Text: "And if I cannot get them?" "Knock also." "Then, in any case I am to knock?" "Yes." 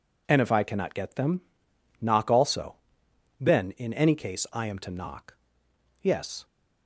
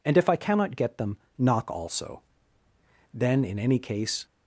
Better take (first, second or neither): first